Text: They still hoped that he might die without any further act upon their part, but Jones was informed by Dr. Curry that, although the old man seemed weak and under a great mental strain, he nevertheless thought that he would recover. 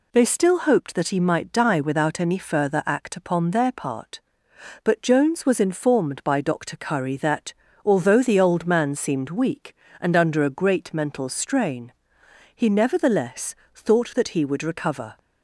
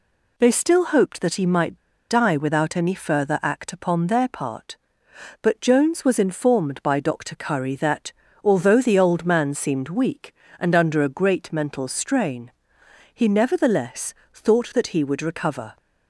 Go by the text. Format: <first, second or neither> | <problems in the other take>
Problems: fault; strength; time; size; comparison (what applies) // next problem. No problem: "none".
first | pauses between "might" and "die"; slight; at 1.7 s; 0.30 s long // pauses between "nevertheless" and "thought"; slight; at 14.1 s; 0.22 s long; slight in the first